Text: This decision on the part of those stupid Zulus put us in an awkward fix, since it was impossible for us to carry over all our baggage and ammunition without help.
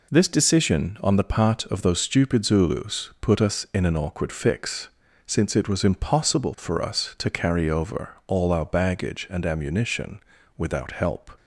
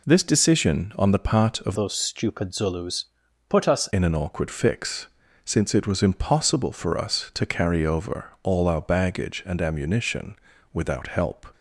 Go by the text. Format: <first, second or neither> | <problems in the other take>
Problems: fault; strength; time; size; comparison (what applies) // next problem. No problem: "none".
first | changes voice from "those" to "us"; from 1.7 to 3.8 s; 2.1 s long // pauses between "Zulus" and "put"; at 3.0 s; 0.42 s long // pauses between "ammunition" and "without"; at 10.3 s; 0.38 s long; also in the first